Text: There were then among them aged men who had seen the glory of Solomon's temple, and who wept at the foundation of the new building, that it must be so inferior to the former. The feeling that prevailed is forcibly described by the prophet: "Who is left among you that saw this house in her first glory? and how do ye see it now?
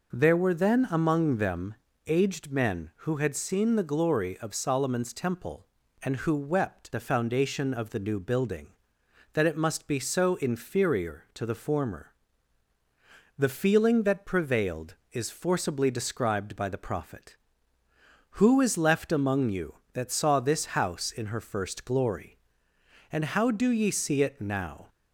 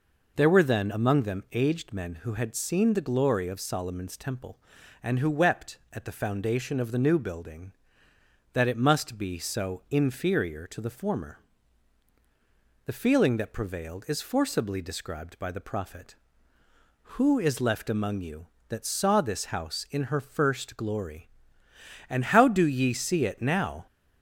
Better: second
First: pauses between "them" and "aged"; slight; at 1.7 s; 0.32 s long // skips "at"; at 6.9 s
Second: none

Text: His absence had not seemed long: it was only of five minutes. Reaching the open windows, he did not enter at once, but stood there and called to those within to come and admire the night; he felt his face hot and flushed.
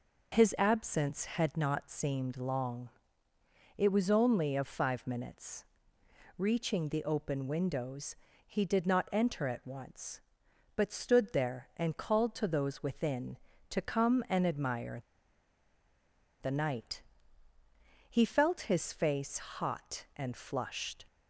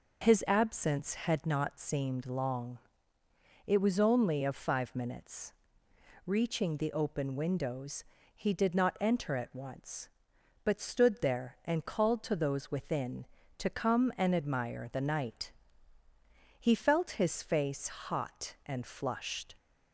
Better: second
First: pauses between "admire" and "the"; strong; at 15.0 s; 1.4 s long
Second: none

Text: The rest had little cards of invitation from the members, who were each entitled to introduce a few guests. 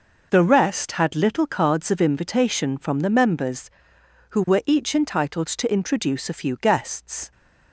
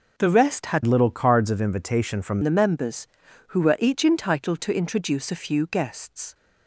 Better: first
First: none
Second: changes voice from "little" to "from"; from 0.8 to 2.3 s; 1.5 s long

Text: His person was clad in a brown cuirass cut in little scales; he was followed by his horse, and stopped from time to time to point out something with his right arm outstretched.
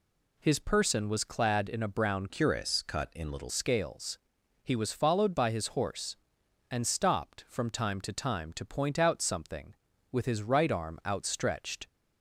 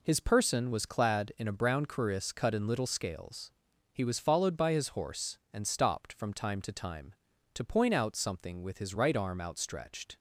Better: second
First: changes voice from "cuirass" to "little"; from 2.2 to 3.5 s; 1.3 s long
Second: none

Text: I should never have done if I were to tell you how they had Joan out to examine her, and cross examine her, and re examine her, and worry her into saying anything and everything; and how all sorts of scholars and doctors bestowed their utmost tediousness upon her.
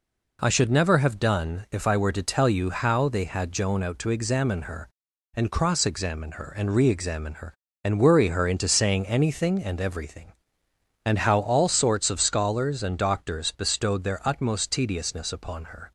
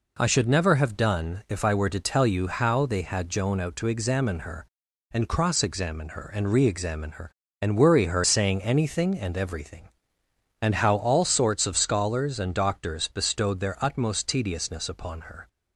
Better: first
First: none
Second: skips "into"; at 8.2 s

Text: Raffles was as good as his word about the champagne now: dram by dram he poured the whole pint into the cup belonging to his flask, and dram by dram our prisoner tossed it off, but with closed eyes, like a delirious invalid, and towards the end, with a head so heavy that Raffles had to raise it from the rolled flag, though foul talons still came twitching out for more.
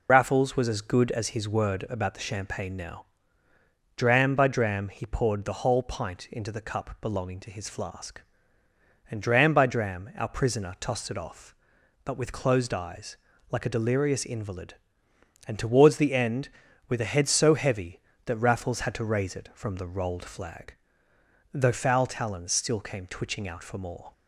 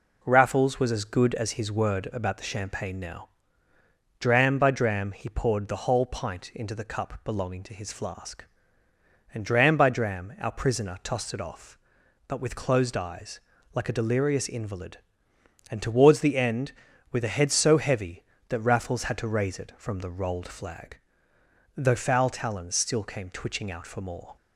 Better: second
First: loses the start of "Raffles"; at 0.0 s; 95 ms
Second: none

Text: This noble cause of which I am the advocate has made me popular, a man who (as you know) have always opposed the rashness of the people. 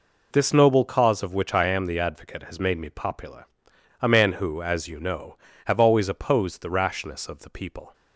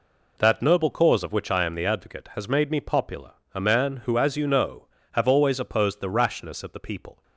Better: first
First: none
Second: says "That" for "This"; at 0.3 s

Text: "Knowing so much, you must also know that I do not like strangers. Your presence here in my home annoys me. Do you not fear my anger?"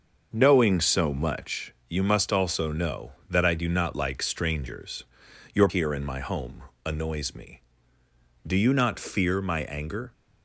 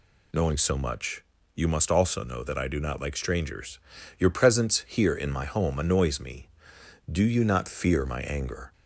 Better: second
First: starts louder than the rest; until 1.3 s; 6 dB // skips "presence"; at 5.6 s // pauses between "home" and "annoys"; slight; at 6.6 s; 0.22 s long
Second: none

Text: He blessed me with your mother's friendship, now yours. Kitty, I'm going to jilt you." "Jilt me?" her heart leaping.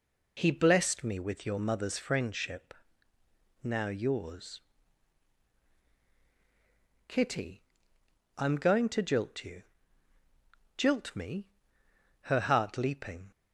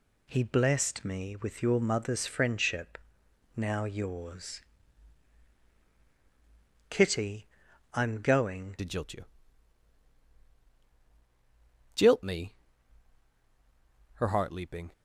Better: first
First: none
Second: changes voice at "to"; from 8.7 s on; 6.2 s long

